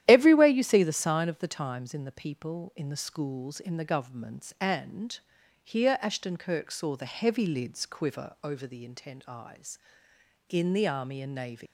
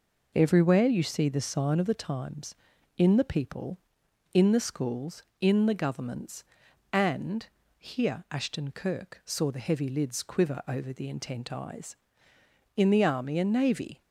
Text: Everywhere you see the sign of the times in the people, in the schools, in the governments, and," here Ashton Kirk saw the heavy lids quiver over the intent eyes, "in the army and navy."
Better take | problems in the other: second | starts louder than the rest; strong; until 1.0 s; 12 dB // leaves "navy" unfinished; at 11.6 s; 135 ms

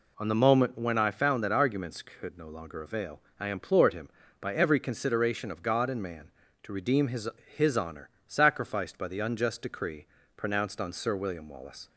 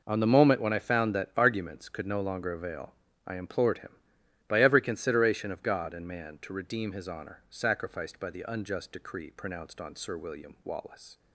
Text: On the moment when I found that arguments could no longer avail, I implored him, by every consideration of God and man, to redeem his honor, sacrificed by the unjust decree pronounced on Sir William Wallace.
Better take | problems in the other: second | says "his" twice; at 7.5 s // pauses between "decree" and "pronounced"; slight; at 10.0 s; 0.30 s long

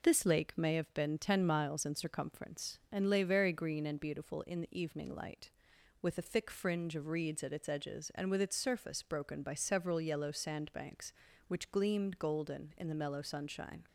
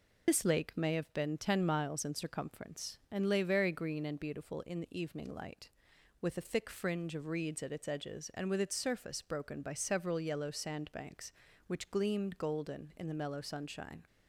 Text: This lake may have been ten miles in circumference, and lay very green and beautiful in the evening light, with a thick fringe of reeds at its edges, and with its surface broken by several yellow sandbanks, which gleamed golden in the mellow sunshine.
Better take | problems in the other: first | loses the start of "This"; at 0.2 s; 50 ms

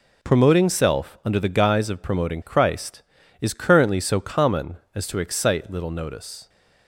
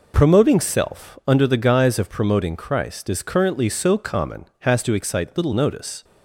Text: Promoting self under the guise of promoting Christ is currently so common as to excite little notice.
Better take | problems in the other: first | says "has" for "as"; at 4.6 s

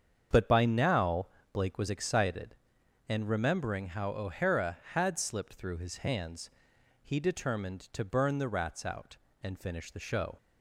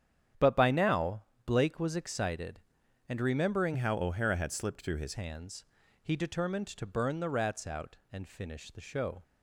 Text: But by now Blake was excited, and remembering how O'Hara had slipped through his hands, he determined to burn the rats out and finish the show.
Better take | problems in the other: first | starts louder than the rest; strong; until 1.6 s; 9.5 dB; strong in the first // pauses between "now" and "Blake"; slight; at 1.2 s; 0.22 s long; slight in the first // changes voice from "how" to "his"; from 3.7 to 5.1 s; 1.4 s long

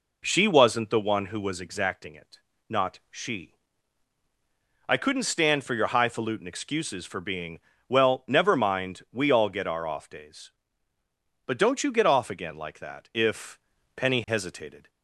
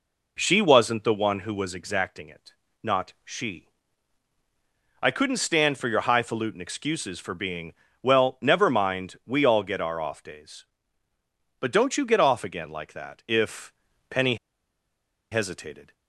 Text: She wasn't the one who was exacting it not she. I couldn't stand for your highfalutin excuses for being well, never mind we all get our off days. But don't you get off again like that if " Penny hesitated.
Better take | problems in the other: first | pauses between "it" and "not"; slight; at 2.5 s; 0.32 s long; slight in the first // pauses between "being" and "well"; slight; at 7.7 s; 0.30 s long; slight in the first // pauses between "Penny" and "hesitated"; noticeable; at 14.3 s; 0.96 s long

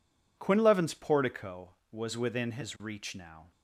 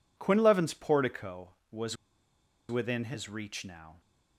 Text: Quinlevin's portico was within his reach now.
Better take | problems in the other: first | pauses between "was" and "within"; noticeable; at 1.9 s; 0.74 s long

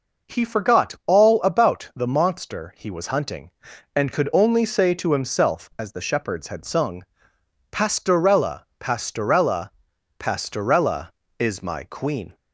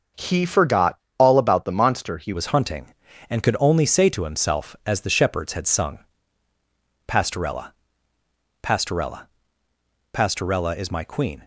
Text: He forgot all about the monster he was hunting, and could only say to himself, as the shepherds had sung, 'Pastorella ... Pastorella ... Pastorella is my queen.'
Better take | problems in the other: first | starts louder than the rest; until 1.3 s; 6.5 dB // pauses between "forgot" and "all"; slight; at 0.9 s; 0.22 s long // changes voice at "was"; from 2.3 s on; 9.1 s long

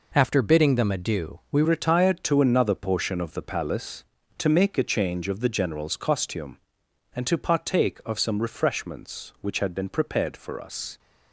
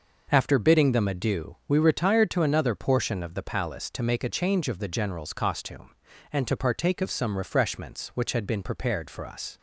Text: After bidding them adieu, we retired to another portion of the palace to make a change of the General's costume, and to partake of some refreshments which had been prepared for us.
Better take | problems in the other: second | changes voice at "retired"; from 1.6 s on; 9.3 s long

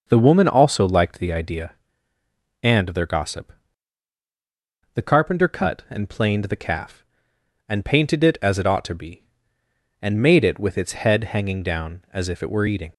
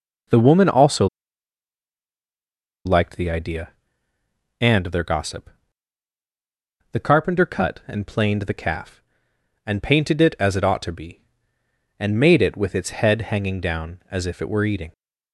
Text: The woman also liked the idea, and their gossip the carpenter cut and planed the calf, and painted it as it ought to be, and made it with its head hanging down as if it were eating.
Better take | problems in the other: first | pauses between "also" and "liked"; strong; at 1.0 s; 1.7 s long // pauses between "gossip" and "the"; strong; at 5.5 s; 1.4 s long; strong in the first

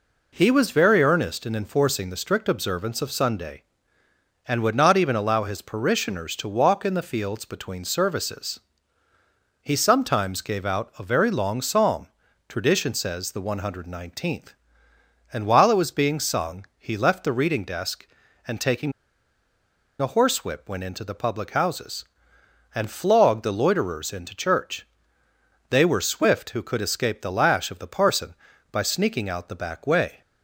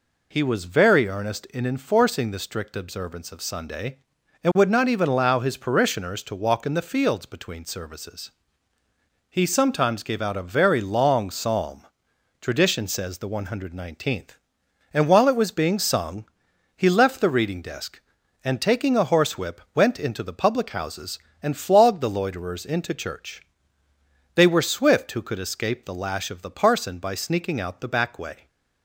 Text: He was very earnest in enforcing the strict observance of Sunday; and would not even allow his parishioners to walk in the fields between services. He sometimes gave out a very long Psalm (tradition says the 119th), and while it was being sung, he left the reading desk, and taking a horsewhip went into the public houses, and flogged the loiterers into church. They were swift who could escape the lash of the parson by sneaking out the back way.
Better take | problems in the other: second | pauses between "taking" and "a"; at 18.9 s; 1.0 s long

